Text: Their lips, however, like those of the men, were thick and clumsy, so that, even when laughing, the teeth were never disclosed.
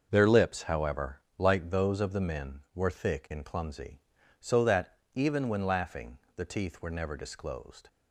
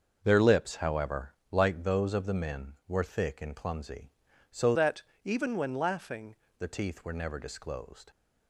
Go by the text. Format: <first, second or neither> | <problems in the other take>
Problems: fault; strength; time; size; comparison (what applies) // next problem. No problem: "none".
first | starts louder than the rest; until 1.2 s; 6.5 dB; also in the first // changes voice from "that" to "laughing"; from 4.7 to 6.3 s; 1.6 s long